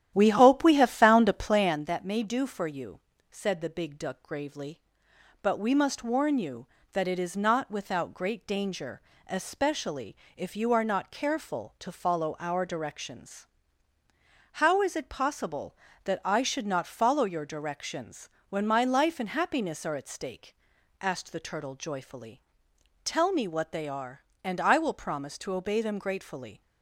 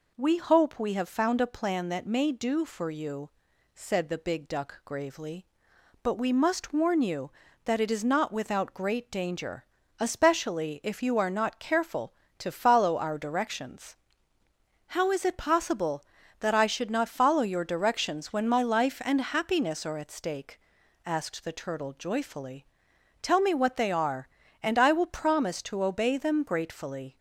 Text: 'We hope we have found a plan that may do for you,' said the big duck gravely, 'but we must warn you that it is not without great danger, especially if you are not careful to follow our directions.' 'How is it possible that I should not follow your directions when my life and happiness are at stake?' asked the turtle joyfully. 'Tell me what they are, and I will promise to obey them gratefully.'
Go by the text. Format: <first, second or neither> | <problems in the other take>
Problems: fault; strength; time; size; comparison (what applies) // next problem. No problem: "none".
second | starts louder than the rest; strong; until 1.8 s; 11.5 dB // pauses between "especially" and "if"; slight; at 10.1 s; 0.22 s long // pauses between "directions" and "when"; slight; at 18.2 s; 0.20 s long